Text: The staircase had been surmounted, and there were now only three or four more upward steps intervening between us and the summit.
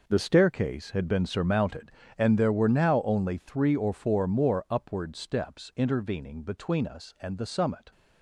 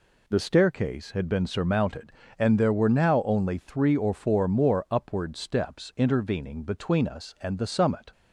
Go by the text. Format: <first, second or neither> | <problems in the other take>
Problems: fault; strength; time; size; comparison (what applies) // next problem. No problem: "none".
second | gets quieter; strong; throughout; 11.5 dB